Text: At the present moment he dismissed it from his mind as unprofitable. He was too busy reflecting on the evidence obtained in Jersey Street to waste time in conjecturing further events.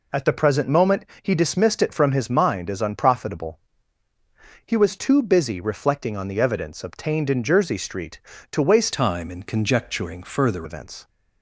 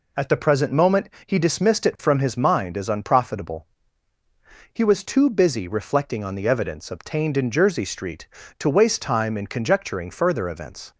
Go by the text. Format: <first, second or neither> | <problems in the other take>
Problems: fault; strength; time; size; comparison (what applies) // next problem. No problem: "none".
second | pauses between "moment" and "he"; slight; at 1.0 s; 0.16 s long; slight in the second // changes voice from "time" to "further"; from 8.9 to 10.6 s; 1.7 s long